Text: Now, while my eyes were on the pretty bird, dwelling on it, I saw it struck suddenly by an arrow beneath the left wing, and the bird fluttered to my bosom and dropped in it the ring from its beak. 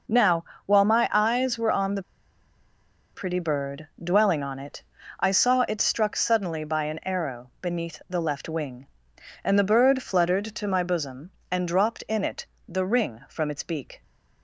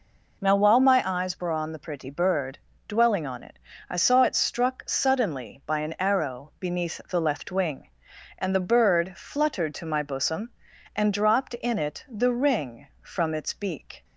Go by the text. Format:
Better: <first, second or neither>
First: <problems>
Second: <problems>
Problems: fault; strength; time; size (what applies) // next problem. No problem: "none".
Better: second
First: pauses between "the" and "pretty"; at 2.0 s; 1.1 s long // pauses between "it" and "the"; slight; at 12.4 s; 0.24 s long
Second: none